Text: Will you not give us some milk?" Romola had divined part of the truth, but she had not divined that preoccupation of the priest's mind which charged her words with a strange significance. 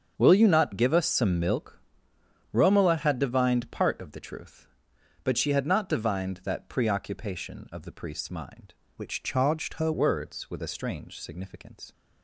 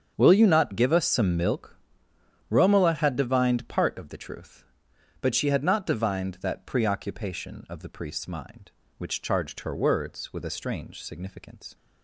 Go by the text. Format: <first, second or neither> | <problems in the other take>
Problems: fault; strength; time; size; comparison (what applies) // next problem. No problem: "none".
second | starts louder than the rest; strong; until 1.1 s; 7 dB; strong in the second // changes voice from "which" to "her"; from 8.9 to 9.9 s; 1.0 s long